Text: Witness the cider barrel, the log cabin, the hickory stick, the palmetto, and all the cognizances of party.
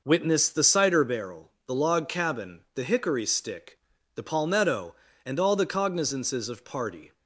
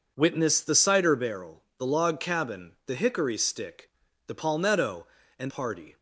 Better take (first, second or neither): first